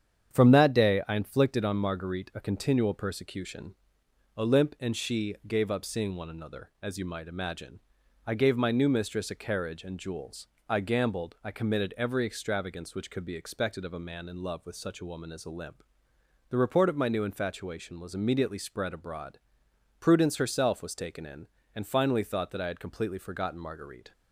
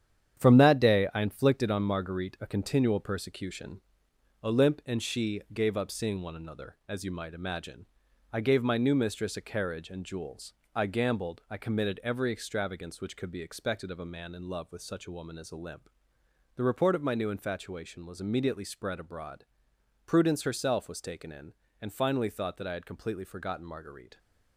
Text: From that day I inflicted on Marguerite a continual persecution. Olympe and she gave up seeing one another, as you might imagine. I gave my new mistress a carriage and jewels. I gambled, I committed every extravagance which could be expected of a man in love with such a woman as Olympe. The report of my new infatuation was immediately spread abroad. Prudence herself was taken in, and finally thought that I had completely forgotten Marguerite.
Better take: first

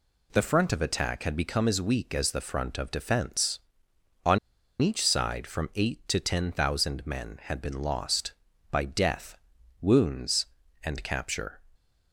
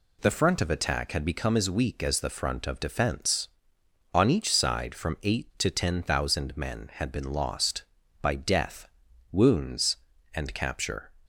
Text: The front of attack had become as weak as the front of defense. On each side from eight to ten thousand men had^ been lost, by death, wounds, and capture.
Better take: second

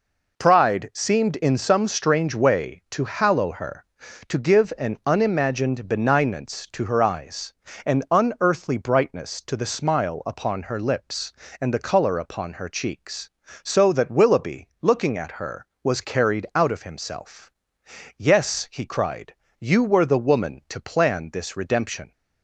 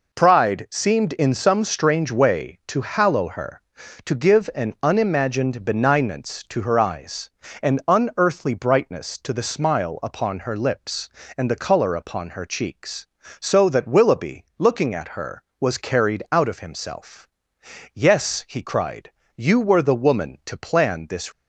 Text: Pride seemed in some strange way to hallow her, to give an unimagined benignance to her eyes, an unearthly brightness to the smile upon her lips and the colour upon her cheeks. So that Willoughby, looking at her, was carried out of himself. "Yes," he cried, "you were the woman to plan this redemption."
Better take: first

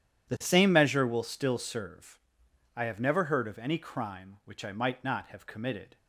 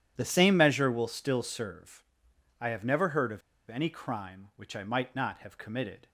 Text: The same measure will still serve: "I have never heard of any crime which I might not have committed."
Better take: first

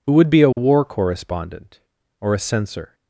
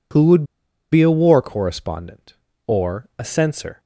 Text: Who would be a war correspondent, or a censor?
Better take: first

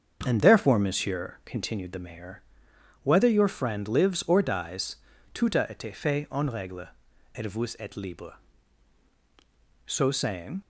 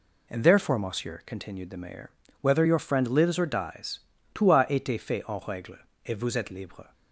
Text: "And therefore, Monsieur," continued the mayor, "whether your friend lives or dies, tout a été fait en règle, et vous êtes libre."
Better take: second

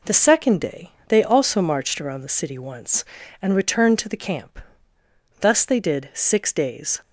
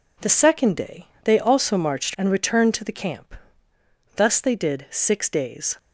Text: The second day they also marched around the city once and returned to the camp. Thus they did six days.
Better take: first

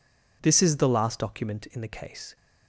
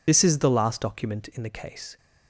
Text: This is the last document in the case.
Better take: first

